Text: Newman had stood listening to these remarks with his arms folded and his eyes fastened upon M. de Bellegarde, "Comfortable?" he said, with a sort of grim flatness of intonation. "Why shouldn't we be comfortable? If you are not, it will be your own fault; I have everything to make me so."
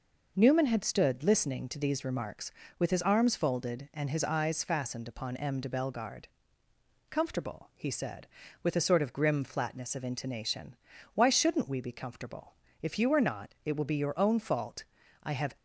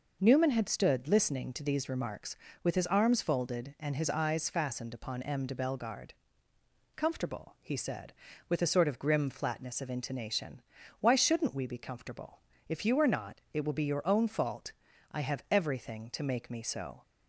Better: second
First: stops before "everything to make me so"; at 15.5 s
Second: none

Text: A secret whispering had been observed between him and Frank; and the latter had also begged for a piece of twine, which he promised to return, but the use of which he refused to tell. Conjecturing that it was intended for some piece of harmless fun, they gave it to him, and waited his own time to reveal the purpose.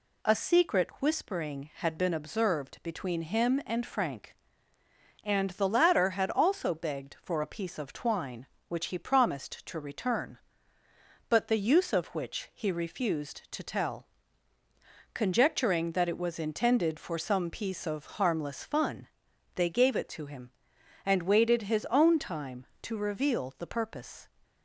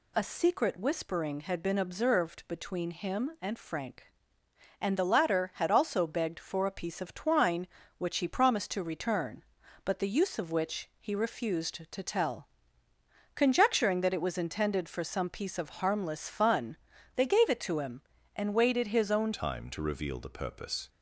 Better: first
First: none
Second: changes voice at "time"; from 19.3 s on; 1.5 s long

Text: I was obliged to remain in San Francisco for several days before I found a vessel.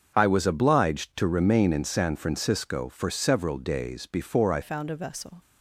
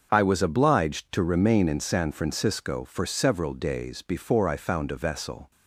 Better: second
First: starts louder than the rest; until 1.1 s; 6.5 dB // changes voice at "found"; from 4.6 s on; 0.7 s long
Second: starts louder than the rest; until 1.1 s; 6.5 dB

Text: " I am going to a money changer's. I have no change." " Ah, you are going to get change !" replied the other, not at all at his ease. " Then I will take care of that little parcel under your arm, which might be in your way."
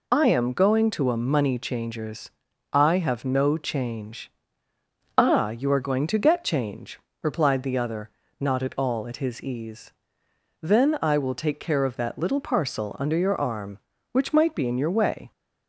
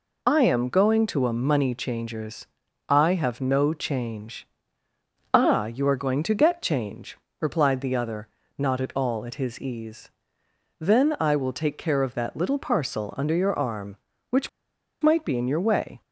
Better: first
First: none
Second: pauses between "which" and "might"; noticeable; at 14.4 s; 0.52 s long

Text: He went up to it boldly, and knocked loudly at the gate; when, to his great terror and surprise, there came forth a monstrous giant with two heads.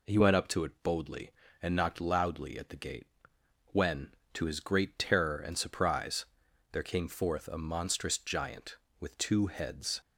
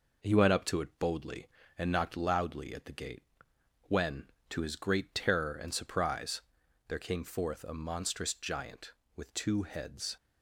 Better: first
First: none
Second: gets quieter; slight; throughout; 2.5 dB

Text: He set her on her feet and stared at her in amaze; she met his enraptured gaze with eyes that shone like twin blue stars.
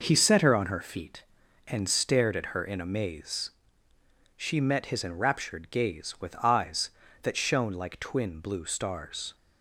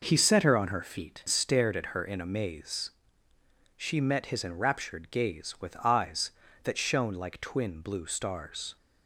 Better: first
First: none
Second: skips "and"; at 1.2 s

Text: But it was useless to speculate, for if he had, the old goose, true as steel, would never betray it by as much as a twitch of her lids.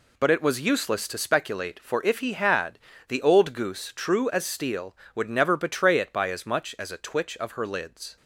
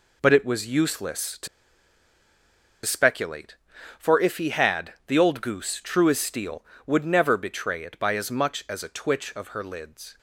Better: first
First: none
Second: pauses between "to" and "speculate"; strong; at 1.4 s; 1.3 s long

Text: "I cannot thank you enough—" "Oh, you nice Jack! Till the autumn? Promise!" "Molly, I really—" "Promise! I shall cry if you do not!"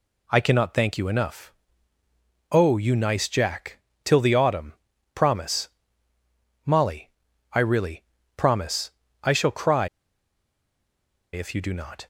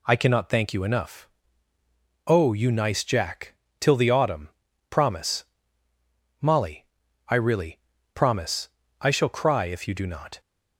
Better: second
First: pauses between "cry" and "if"; strong; at 9.8 s; 1.4 s long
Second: none

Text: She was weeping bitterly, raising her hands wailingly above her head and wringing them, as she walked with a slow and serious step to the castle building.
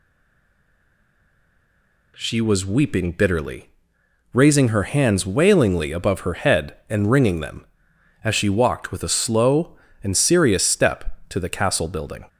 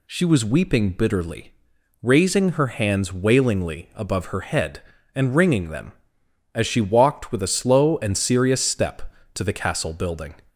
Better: second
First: stays silent before the first word; until 2.1 s; 2.1 s long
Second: none

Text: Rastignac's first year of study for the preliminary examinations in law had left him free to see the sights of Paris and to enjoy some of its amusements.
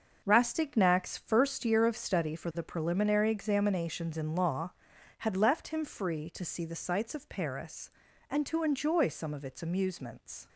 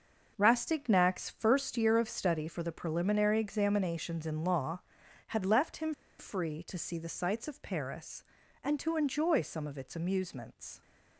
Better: first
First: starts louder than the rest; until 1.2 s; 6 dB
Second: starts louder than the rest; noticeable; until 1.3 s; 6 dB // pauses between "him" and "free"; slight; at 5.9 s; 0.26 s long

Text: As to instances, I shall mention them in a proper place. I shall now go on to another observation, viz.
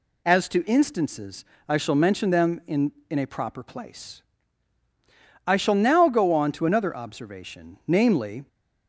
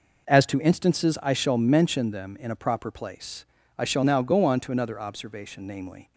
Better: second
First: says "in" twice; at 3.1 s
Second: none

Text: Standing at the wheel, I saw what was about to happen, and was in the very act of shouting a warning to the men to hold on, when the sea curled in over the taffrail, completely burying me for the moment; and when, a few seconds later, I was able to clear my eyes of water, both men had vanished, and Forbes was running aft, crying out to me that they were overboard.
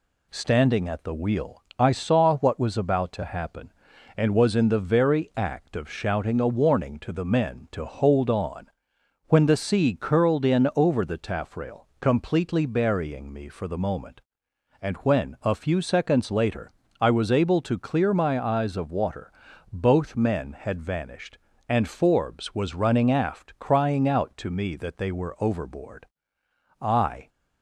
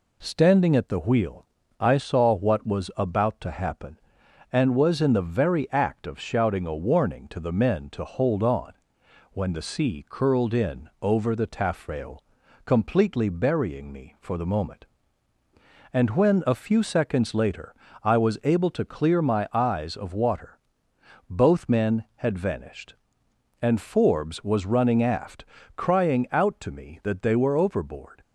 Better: second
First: goes on to say "I"; slight; from 26.8 s on; 0.48 s long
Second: none

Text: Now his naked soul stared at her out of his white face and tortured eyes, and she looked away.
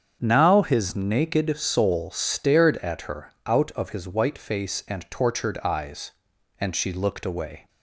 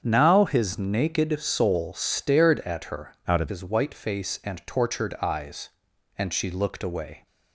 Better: first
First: starts louder than the rest; strong; until 1.2 s; 7.5 dB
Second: starts louder than the rest; strong; until 1.0 s; 7.5 dB // changes voice from "out" to "of"; from 3.2 to 3.5 s; 0.3 s long

